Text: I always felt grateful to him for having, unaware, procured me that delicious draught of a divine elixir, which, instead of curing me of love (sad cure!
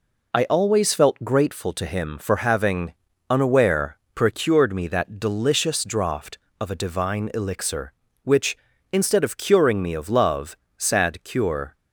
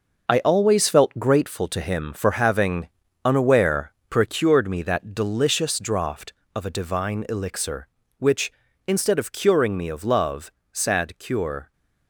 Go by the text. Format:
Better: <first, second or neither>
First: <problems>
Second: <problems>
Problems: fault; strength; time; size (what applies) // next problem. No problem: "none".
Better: first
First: none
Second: gets quieter; strong; throughout; 9 dB